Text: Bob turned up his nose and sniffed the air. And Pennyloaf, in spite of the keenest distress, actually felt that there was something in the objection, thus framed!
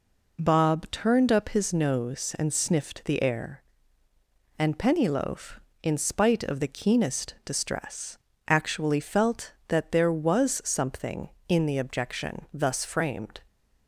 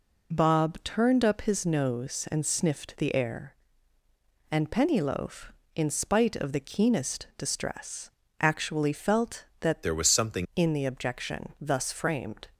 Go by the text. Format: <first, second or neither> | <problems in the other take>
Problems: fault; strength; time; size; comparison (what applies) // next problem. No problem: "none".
first | changes voice from "there" to "something"; from 9.8 to 10.4 s; 0.6 s long